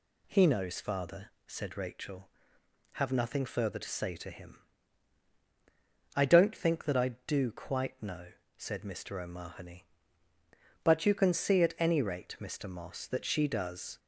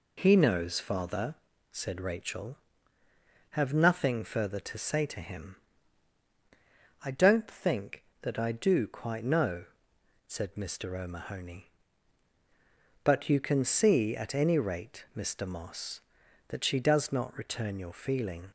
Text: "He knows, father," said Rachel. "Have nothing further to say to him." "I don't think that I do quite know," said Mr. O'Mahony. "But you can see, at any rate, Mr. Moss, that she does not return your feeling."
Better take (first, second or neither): second